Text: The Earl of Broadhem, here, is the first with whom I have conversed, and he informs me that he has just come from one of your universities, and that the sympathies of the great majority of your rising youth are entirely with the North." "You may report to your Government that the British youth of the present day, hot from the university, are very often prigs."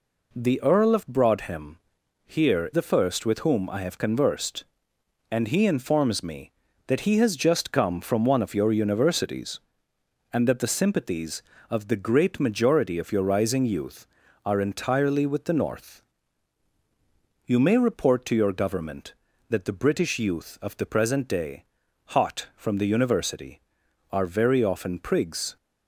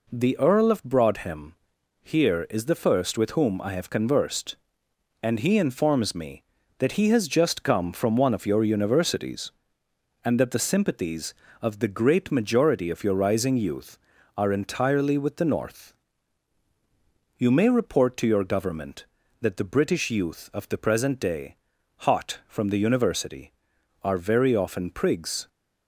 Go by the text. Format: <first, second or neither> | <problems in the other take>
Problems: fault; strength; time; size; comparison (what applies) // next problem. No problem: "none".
second | skips "is"; at 2.7 s